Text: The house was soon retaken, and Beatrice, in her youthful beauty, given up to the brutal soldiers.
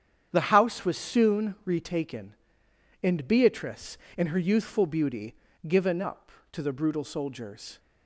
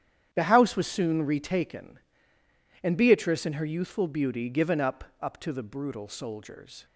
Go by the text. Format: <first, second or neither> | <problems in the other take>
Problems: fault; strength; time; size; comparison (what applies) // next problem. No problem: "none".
first | starts louder than the rest; strong; until 1.3 s; 9.5 dB; strong in the first // says "up" twice; at 5.1 s